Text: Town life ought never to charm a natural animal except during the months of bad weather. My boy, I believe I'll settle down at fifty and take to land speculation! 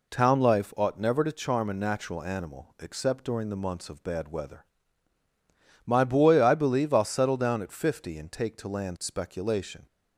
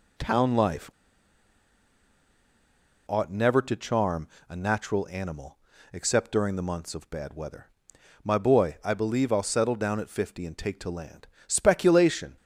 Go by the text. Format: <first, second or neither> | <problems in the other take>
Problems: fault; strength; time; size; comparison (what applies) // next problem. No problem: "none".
first | pauses between "life" and "ought"; strong; at 0.8 s; 2.1 s long // pauses between "charm" and "a"; slight; at 4.2 s; 0.20 s long // pauses between "animal" and "except"; slight; at 5.5 s; 0.34 s long // pauses between "land" and "speculation"; slight; at 11.2 s; 0.22 s long